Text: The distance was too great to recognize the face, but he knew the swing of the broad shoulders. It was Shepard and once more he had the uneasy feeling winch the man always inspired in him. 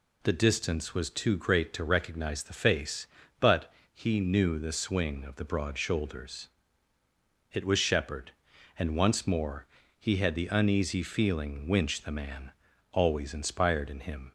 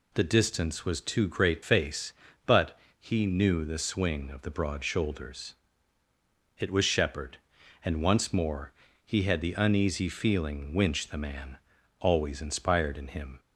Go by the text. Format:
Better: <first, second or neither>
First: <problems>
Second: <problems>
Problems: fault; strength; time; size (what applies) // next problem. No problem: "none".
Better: first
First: pauses between "but" and "he"; slight; at 3.7 s; 0.18 s long // pauses between "more" and "he"; slight; at 9.6 s; 0.34 s long // pauses between "man" and "always"; at 12.5 s; 0.40 s long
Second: skips "to recognize the"; at 1.6 s // pauses between "but" and "he"; slight; at 2.7 s; 0.18 s long // pauses between "more" and "he"; slight; at 8.7 s; 0.34 s long // pauses between "man" and "always"; at 11.5 s; 0.42 s long